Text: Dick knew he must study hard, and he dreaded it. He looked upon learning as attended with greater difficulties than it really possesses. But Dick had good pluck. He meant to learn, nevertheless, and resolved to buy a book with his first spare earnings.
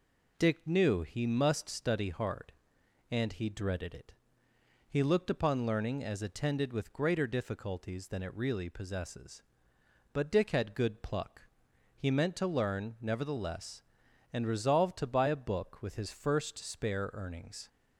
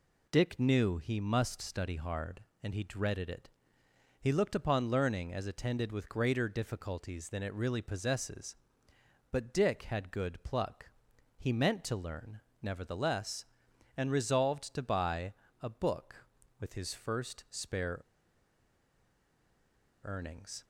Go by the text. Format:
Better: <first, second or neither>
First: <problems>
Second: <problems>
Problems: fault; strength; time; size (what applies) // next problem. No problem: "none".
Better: first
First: none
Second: pauses between "buy" and "a"; slight; at 15.3 s; 0.30 s long // pauses between "spare" and "earnings"; strong; at 18.0 s; 2.0 s long